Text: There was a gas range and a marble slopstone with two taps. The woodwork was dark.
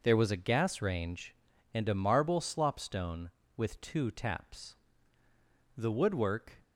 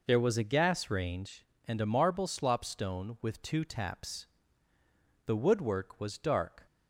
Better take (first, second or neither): second